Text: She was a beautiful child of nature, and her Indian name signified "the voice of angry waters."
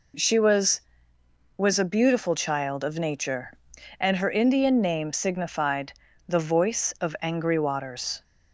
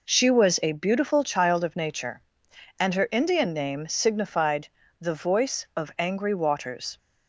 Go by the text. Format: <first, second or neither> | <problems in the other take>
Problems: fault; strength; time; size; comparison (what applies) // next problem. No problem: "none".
second | says "was" twice; at 1.5 s // pauses between "signified" and "the"; slight; at 5.9 s; 0.34 s long; slight in the second